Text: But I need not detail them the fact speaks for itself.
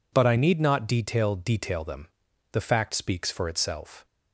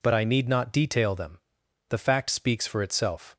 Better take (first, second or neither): second